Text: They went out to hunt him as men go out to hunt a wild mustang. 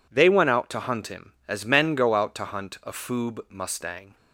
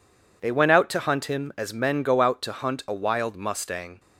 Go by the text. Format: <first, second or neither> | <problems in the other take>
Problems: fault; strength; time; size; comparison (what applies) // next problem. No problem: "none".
second | says "foob" for "wild"; at 2.9 s